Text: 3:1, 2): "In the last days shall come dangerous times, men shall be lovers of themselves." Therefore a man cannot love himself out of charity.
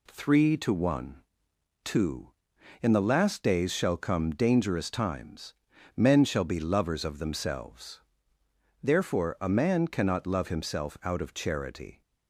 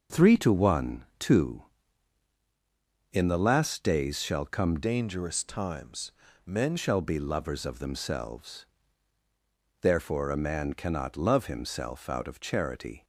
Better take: first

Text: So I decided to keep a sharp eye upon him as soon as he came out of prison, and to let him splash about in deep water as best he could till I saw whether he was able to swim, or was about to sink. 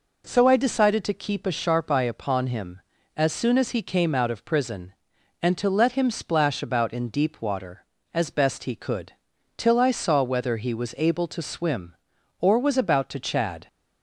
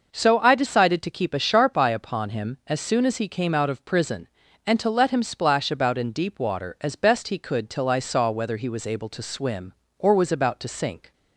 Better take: second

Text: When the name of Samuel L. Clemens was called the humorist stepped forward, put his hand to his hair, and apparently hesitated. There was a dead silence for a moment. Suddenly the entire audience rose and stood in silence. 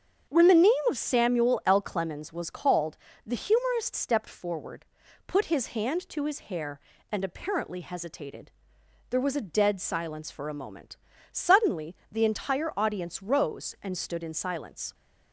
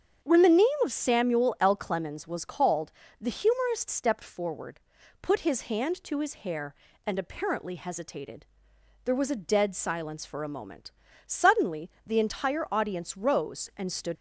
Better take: first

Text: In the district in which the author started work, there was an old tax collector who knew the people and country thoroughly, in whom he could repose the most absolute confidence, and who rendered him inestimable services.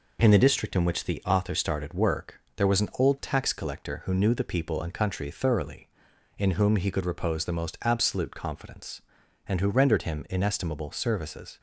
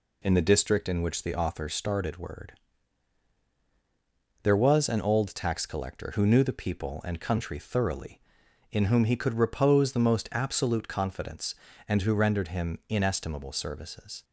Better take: first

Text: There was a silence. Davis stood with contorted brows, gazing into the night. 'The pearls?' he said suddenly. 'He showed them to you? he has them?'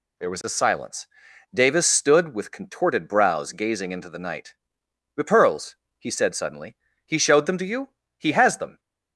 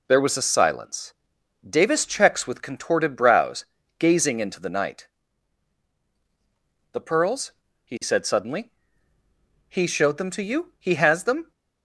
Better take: first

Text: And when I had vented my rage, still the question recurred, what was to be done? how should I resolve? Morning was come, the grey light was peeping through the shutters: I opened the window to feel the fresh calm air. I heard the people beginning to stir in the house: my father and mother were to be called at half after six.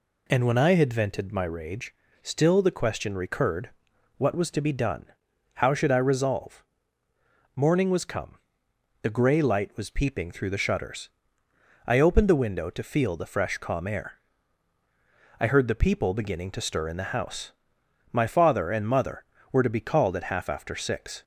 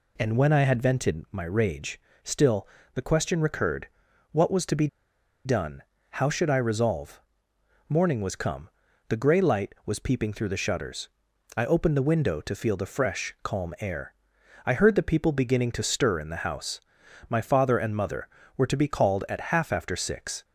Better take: first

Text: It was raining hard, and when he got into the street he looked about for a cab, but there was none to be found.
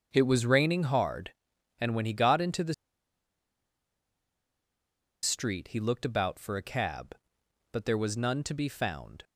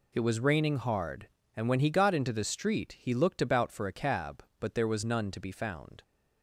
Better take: second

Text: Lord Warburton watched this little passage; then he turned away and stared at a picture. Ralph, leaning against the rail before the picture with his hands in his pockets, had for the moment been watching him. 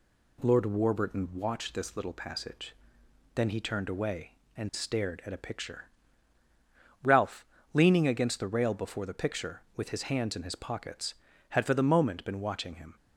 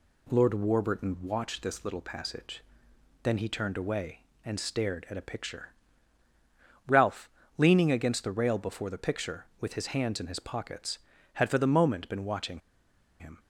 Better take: first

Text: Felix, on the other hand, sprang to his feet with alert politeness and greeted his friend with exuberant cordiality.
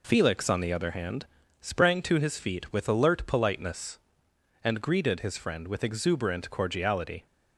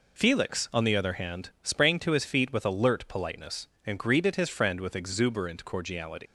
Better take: first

